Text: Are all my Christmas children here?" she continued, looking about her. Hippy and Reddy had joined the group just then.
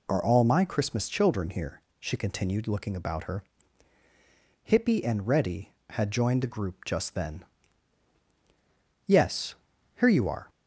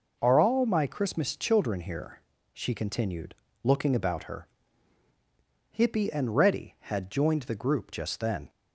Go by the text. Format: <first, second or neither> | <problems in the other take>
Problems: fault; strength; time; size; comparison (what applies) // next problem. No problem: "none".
second | goes on to say "Yes here you are"; from 9.0 s on; 1.4 s long